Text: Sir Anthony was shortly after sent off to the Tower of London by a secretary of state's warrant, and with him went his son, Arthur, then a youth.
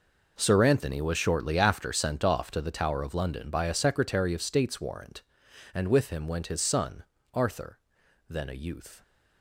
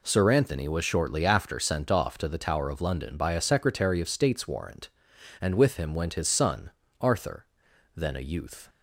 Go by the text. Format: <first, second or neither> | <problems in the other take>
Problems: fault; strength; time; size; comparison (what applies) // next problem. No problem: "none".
second | gets quieter; strong; throughout; 14.5 dB